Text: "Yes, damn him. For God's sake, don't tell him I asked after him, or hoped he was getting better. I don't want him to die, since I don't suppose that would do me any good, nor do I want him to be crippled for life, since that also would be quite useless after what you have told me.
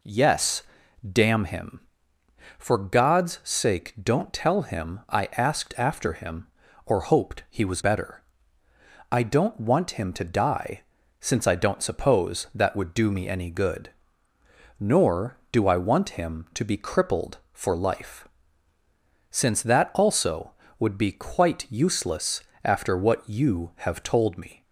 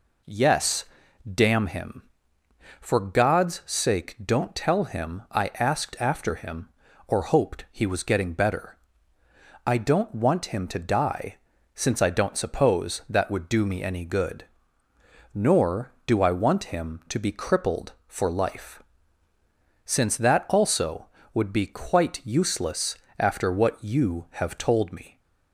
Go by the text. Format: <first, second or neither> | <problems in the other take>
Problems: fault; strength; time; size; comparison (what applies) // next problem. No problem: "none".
second | skips "getting"; at 7.8 s // pauses between "useless" and "after"; slight; at 22.4 s; 0.22 s long; slight in the second